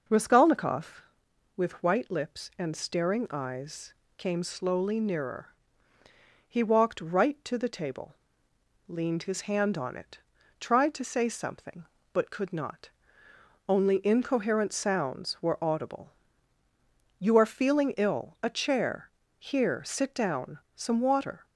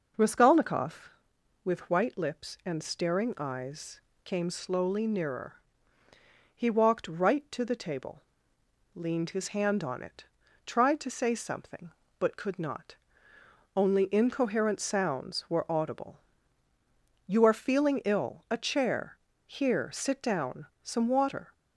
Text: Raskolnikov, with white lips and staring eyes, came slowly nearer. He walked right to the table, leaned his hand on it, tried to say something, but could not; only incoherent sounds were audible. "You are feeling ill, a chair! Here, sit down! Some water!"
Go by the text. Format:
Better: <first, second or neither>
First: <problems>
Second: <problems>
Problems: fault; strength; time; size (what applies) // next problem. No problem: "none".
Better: neither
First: none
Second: none